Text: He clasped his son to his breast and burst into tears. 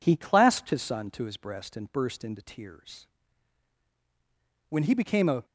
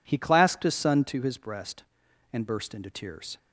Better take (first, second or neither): second